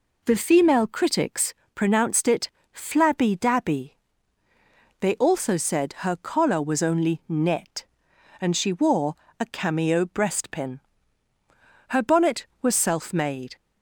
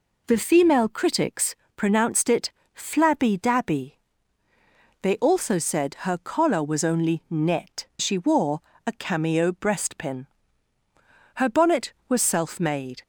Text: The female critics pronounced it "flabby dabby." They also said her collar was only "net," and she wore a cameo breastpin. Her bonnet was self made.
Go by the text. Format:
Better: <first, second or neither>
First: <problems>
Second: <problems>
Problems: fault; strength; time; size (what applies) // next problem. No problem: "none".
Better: first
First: pauses between "critics" and "pronounced"; slight; at 1.5 s; 0.22 s long // pauses between "it" and "flabby"; slight; at 2.4 s; 0.24 s long // pauses between "wore" and "a"; slight; at 9.1 s; 0.23 s long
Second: pauses between "critics" and "pronounced"; slight; at 1.5 s; 0.22 s long // pauses between "it" and "flabby"; slight; at 2.5 s; 0.24 s long // skips "and"; at 7.9 s // pauses between "wore" and "a"; slight; at 8.6 s; 0.24 s long